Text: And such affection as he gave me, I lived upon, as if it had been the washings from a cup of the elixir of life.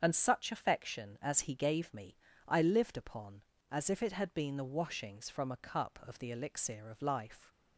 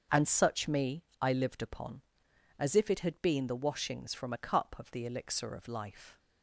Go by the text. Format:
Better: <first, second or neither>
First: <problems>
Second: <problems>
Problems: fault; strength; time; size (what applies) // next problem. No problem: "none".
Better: first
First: starts louder than the rest; strong; until 1.0 s; 7.5 dB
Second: starts louder than the rest; until 1.3 s; 6.5 dB // skips "affection as he gave"; at 0.6 s